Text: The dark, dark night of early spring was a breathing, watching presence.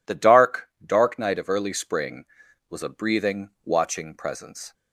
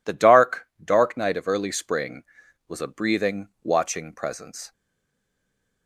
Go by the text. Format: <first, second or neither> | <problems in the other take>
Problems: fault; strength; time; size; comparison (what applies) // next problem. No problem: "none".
first | stays silent after the last word; from 4.7 s on; 1.1 s long